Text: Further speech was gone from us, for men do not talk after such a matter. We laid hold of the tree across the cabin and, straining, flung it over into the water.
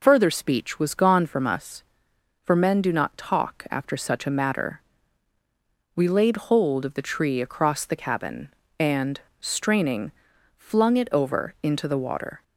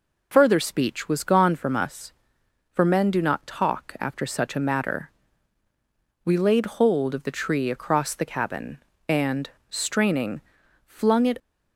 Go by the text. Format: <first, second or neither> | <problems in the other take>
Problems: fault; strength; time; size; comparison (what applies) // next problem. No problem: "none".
first | stops before "over into the water"; at 11.3 s